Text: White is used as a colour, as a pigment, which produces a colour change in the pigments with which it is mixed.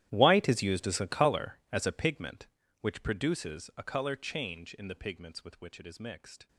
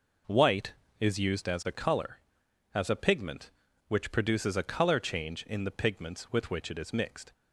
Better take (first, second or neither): second